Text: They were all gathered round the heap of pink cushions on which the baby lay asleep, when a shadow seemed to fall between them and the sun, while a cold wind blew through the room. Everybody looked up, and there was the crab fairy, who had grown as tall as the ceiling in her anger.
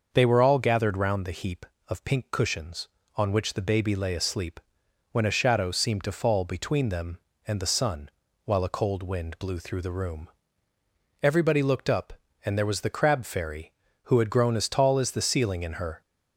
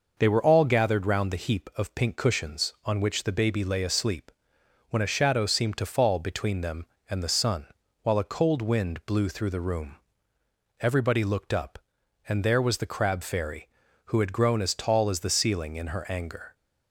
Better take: second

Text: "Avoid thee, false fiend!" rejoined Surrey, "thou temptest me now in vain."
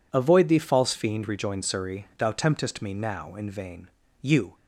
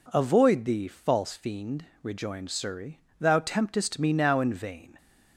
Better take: second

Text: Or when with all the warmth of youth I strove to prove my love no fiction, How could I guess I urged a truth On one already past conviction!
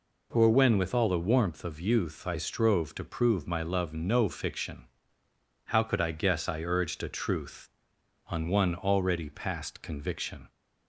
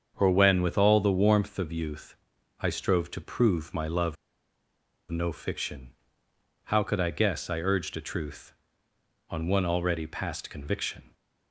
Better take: first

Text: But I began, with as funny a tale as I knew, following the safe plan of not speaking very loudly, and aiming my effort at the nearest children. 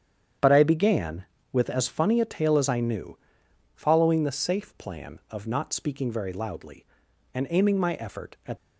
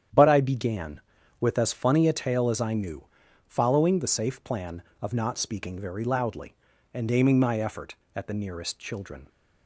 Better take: second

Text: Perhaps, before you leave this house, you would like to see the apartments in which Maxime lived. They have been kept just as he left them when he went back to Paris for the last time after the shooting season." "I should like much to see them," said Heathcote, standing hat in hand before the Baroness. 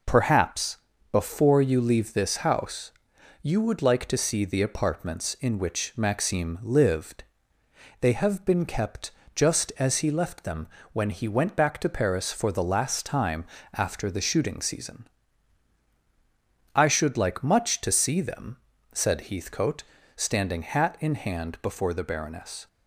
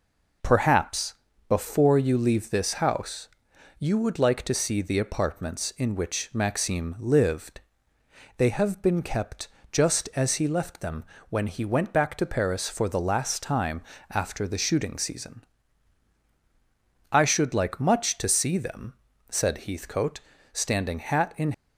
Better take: first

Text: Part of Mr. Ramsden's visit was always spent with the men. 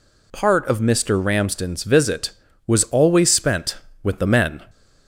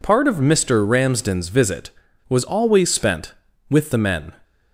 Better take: neither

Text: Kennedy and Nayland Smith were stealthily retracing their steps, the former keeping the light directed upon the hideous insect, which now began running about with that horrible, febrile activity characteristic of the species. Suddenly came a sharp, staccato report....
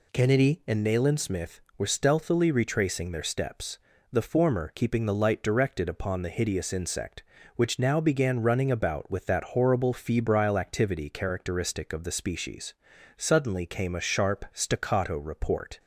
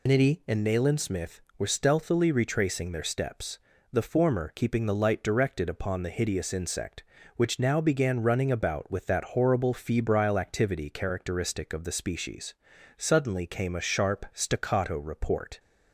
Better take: first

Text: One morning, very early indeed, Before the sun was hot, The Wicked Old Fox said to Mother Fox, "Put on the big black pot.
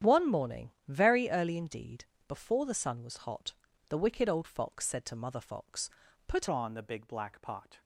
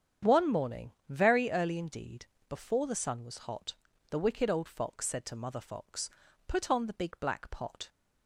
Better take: second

